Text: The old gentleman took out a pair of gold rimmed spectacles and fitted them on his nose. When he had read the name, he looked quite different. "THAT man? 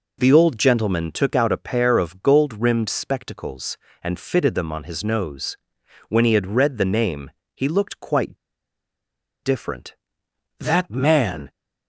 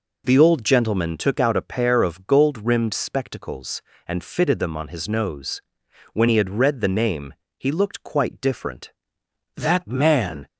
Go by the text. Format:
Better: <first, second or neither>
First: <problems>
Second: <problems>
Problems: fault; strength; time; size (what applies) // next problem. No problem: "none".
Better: second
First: pauses between "quite" and "different"; at 8.3 s; 1.0 s long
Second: none